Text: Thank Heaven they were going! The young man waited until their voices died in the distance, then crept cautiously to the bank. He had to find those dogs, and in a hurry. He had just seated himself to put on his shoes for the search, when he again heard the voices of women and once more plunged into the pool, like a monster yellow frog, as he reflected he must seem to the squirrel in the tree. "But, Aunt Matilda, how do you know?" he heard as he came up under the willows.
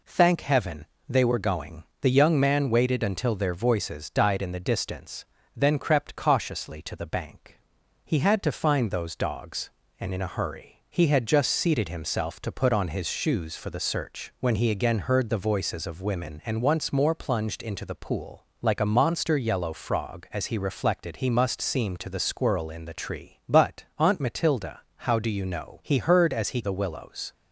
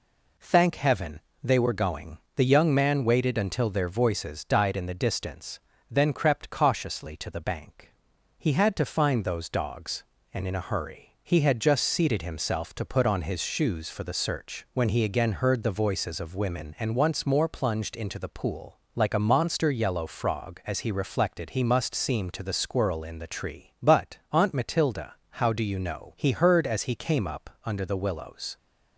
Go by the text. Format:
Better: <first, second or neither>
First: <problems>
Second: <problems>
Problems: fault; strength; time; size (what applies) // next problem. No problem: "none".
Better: second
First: pauses between "Heaven" and "they"; slight; at 0.8 s; 0.24 s long // skips "came up under"; at 26.6 s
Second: pauses between "Heaven" and "they"; slight; at 1.1 s; 0.24 s long